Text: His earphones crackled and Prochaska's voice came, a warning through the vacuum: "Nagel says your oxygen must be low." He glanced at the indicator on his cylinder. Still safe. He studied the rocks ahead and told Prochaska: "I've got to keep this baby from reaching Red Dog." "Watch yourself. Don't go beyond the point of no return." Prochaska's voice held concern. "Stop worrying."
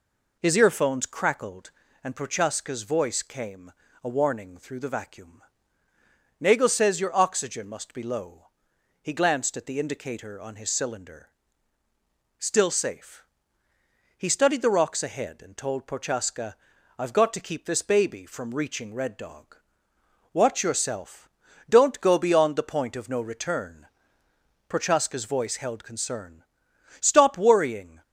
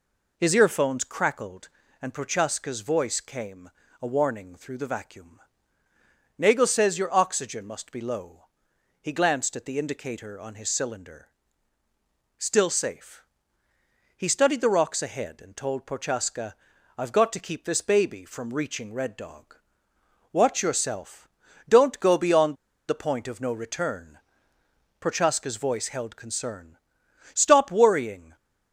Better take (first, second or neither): first